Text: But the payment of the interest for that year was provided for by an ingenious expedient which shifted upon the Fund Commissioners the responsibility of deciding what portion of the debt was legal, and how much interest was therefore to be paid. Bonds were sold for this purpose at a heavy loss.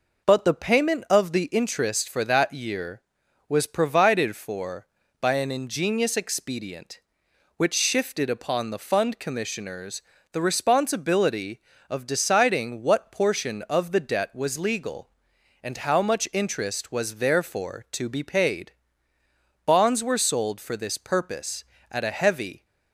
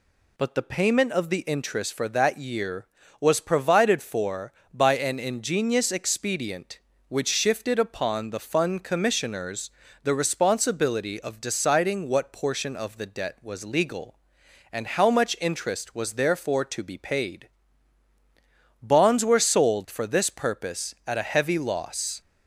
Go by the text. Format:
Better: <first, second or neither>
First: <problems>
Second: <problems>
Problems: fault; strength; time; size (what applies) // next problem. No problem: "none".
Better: second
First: pauses between "Commissioners" and "the"; slight; at 10.0 s; 0.30 s long // stops before "loss"; at 22.6 s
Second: pauses between "Commissioners" and "the"; slight; at 9.7 s; 0.32 s long